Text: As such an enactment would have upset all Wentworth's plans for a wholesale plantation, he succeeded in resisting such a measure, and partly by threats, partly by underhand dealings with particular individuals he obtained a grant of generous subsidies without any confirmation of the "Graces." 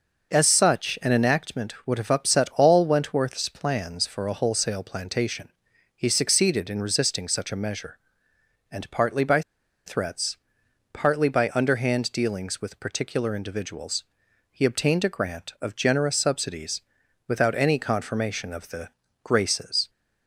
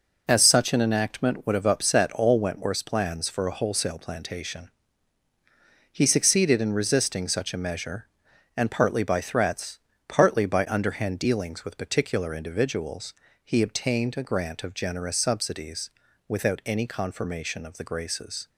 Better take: second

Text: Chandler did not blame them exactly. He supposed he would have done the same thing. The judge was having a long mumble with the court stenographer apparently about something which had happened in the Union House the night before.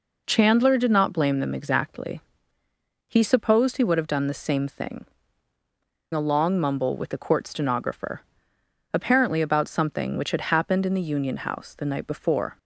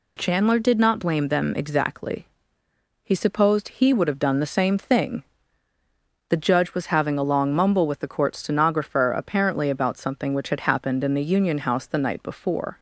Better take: second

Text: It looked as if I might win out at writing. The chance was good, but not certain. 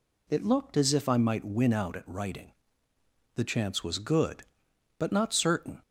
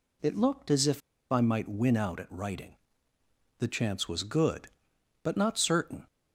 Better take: first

